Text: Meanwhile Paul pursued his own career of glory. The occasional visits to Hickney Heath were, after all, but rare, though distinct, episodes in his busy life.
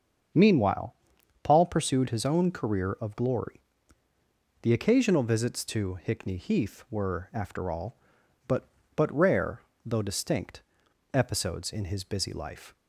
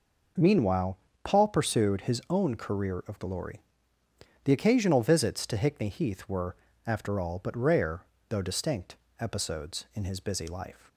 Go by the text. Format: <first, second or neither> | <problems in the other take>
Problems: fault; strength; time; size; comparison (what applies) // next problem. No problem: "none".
second | starts louder than the rest; until 1.8 s; 7 dB // pauses between "Meanwhile" and "Paul"; noticeable; at 0.9 s; 0.48 s long; slight in the second // says "but" twice; at 8.9 s